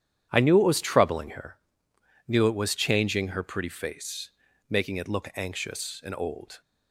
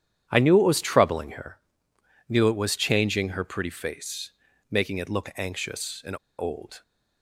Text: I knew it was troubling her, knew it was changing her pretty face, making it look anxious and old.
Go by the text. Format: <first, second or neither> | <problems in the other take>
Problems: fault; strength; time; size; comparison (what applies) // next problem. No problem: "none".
first | starts louder than the rest; strong; until 1.3 s; 10 dB; strong in the first // pauses between "and" and "old"; slight; at 6.1 s; 0.23 s long